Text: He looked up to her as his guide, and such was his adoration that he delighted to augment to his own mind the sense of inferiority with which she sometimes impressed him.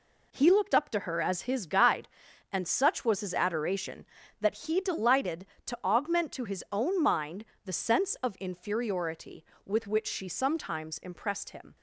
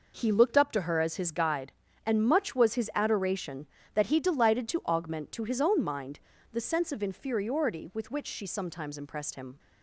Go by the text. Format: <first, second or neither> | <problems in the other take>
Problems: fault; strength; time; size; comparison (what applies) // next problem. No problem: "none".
first | says "much" for "such"; at 2.2 s // pauses between "mind" and "the"; slight; at 6.2 s; 0.32 s long; slight in the first